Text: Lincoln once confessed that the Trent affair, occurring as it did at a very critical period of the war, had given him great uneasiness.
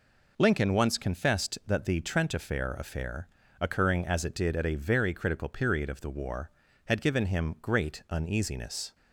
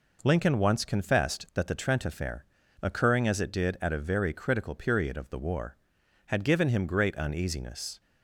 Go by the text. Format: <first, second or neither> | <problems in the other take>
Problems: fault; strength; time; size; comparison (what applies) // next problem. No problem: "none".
second | says "affair" twice; at 2.7 s